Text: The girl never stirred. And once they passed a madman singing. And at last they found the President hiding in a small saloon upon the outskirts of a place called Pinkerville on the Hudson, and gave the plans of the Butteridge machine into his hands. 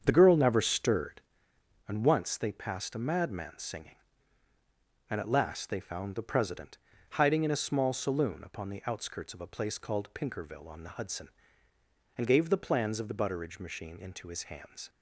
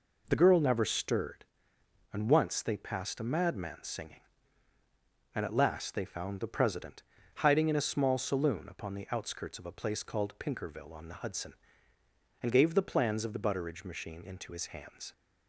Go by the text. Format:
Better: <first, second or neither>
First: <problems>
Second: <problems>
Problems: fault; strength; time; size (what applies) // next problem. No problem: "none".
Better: second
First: starts louder than the rest; strong; until 1.6 s; 7.5 dB // pauses between "President" and "hiding"; slight; at 6.7 s; 0.34 s long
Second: pauses between "President" and "hiding"; slight; at 7.0 s; 0.34 s long